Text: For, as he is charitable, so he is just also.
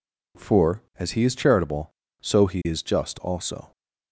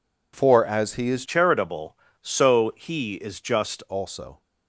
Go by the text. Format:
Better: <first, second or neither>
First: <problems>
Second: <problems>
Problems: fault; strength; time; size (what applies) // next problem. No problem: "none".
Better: first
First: none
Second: changes voice from "charitable" to "just"; from 1.2 to 3.8 s; 2.6 s long